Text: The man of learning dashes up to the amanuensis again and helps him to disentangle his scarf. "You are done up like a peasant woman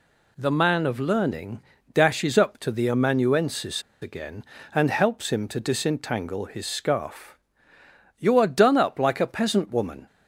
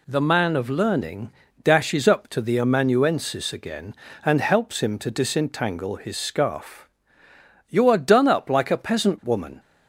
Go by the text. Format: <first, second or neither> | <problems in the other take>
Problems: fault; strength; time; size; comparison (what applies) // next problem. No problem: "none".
second | pauses between "learning" and "dashes"; slight; at 1.6 s; 0.32 s long; slight in the second // pauses between "amanuensis" and "again"; slight; at 3.8 s; 0.21 s long